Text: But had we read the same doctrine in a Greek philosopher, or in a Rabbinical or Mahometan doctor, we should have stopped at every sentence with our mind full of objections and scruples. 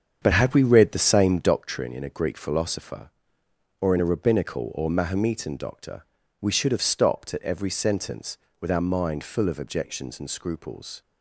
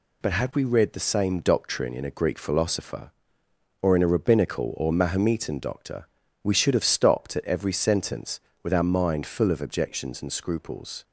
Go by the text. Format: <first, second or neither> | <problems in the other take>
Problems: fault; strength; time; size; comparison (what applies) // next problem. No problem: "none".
second | starts louder than the rest; strong; until 1.6 s; 7.5 dB